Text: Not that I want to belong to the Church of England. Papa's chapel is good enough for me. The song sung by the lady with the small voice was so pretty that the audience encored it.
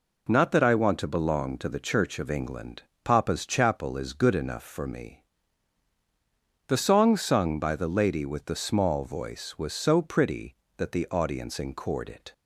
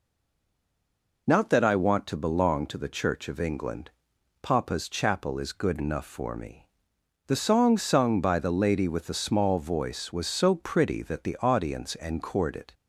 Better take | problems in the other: first | stays silent before the first word; noticeable; until 1.2 s; 1.2 s long

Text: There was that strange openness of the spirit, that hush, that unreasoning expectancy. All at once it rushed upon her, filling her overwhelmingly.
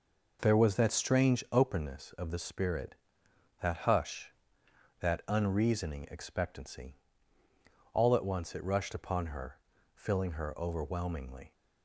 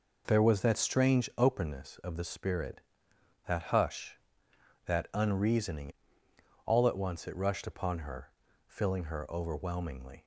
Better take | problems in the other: first | skips "expectancy"; at 6.2 s

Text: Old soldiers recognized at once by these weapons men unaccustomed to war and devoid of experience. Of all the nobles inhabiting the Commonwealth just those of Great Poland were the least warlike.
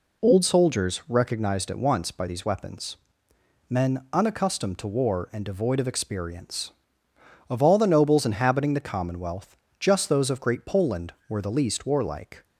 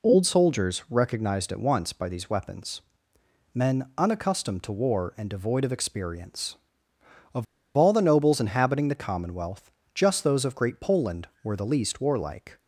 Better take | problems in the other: first | pauses between "weapons" and "men"; noticeable; at 2.8 s; 0.72 s long; noticeable in the first // pauses between "Of" and "all"; slight; at 7.4 s; 0.33 s long // pauses between "Commonwealth" and "just"; slight; at 9.7 s; 0.20 s long; slight in the first

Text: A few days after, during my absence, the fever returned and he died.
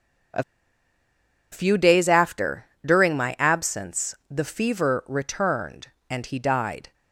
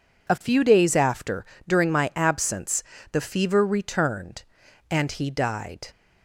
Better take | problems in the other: second | pauses between "A" and "few"; at 0.4 s; 1.0 s long

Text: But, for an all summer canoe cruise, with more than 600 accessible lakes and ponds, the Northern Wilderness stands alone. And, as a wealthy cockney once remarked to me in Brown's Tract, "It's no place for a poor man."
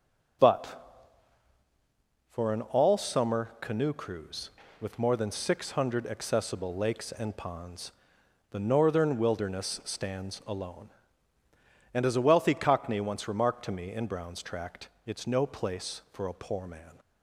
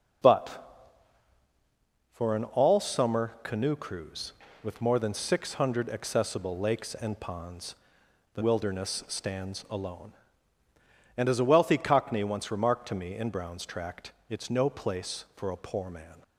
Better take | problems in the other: first | skips "Northern"; at 8.4 s

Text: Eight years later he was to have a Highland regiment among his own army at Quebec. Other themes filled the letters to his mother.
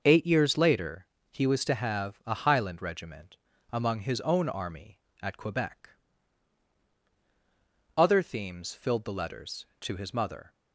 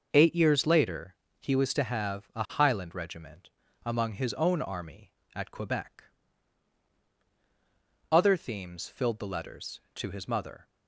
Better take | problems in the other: neither | pauses between "later" and "he"; slight; the same in both // pauses between "regiment" and "among"; slight; the same in both

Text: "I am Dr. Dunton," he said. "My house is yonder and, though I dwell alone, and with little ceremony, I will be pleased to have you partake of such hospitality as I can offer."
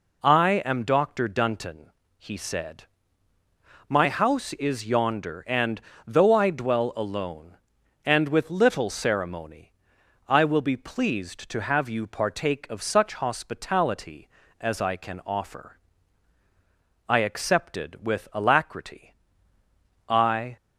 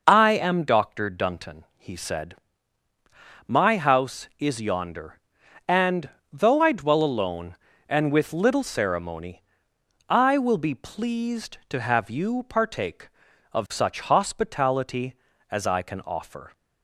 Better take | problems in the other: second | goes on to say "I accepted with alacrity I"; strong; from 17.0 s on; 3.4 s long

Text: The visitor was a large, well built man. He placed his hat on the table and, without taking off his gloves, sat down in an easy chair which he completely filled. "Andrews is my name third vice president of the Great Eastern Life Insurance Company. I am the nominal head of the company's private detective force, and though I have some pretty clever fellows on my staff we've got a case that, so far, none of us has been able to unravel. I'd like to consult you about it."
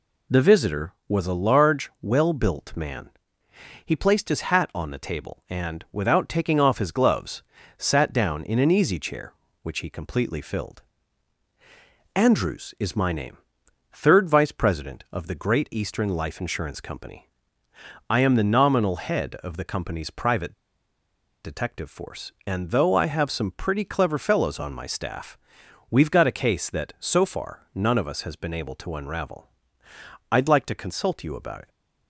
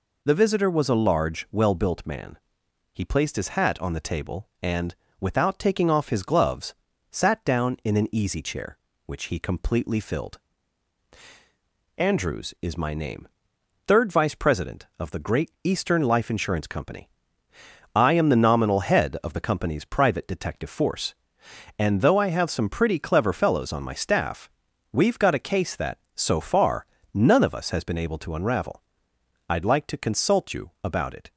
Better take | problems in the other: second | pauses between "name" and "third"; noticeable; at 13.3 s; 0.52 s long; noticeable in the second // pauses between "private" and "detective"; noticeable; at 20.5 s; 0.91 s long // pauses between "staff" and "we've"; noticeable; at 25.3 s; 0.54 s long; also in the second

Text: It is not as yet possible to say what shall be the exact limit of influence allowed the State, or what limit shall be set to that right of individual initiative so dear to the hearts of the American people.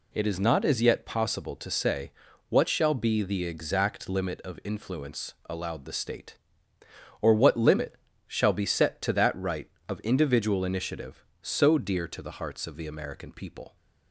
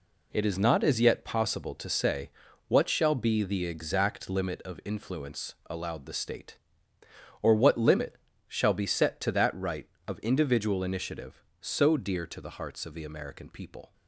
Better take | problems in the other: first | gets quieter; strong; throughout; 8.5 dB // pauses between "say" and "what"; at 2.3 s; 0.38 s long; also in the first // pauses between "limit" and "shall"; slight; at 8.1 s; 0.30 s long; slight in the first

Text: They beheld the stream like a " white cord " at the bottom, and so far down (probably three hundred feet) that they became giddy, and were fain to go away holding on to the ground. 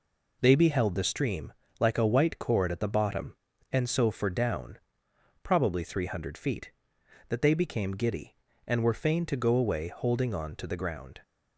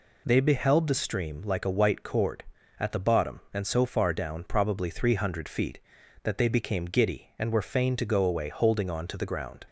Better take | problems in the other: second | pauses between "stream" and "like"; slight; at 1.5 s; 0.28 s long // says "for" for "far"; at 4.0 s

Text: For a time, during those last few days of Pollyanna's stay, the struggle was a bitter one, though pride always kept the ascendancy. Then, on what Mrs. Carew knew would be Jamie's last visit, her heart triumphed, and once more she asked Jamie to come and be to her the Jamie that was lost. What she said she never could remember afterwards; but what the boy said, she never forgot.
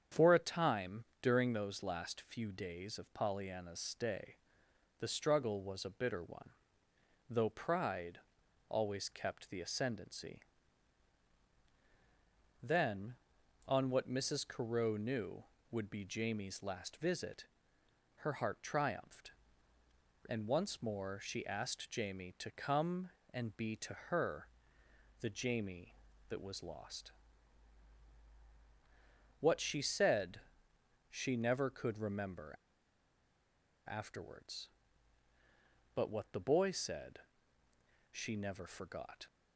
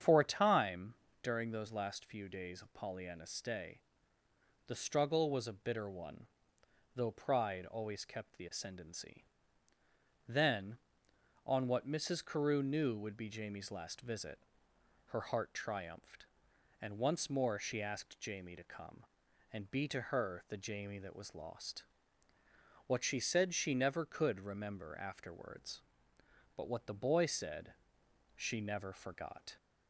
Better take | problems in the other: second | starts louder than the rest; strong; until 1.3 s; 8 dB; strong in the second // pauses between "pride" and "always"; noticeable; at 8.1 s; 0.50 s long // pauses between "to" and "her"; slight; at 23.9 s; 0.16 s long // pauses between "her" and "the"; noticeable; at 24.4 s; 0.74 s long // pauses between "said" and "she"; noticeable; at 30.3 s; 0.72 s long // pauses between "remember" and "afterwards"; strong; at 32.5 s; 1.3 s long

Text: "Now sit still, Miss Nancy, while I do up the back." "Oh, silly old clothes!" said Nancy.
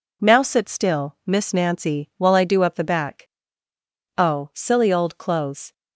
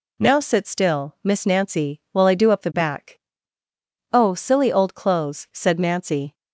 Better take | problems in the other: second | stops before "said Nancy"; at 5.7 s

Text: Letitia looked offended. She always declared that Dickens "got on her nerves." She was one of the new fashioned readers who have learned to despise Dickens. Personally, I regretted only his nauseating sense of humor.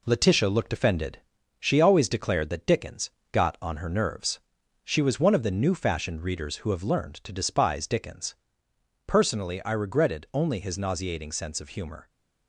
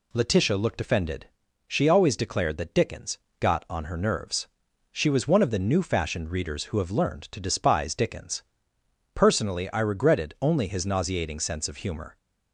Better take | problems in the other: second | gets quieter; noticeable; throughout; 4.5 dB // pauses between "Dickens" and "got"; slight; at 3.0 s; 0.22 s long; slight in the second

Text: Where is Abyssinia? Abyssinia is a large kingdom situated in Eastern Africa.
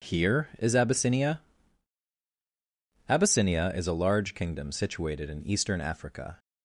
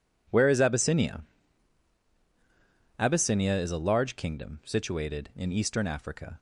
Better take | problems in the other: second | says "Here" for "Where"; at 0.0 s

